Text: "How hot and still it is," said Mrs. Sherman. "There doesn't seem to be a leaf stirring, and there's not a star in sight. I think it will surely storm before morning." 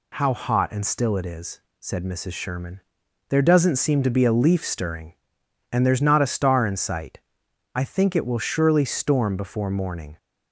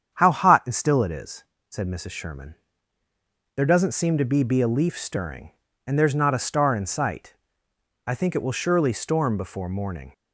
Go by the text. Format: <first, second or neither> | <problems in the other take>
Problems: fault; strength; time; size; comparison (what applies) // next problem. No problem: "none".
first | starts louder than the rest; strong; until 1.1 s; 8.5 dB // says "be" twice; at 4.4 s